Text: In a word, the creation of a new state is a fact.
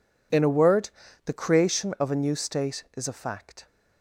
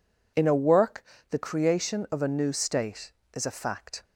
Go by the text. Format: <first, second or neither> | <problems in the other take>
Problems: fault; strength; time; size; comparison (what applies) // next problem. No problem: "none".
first | says "work" for "word"; at 0.5 s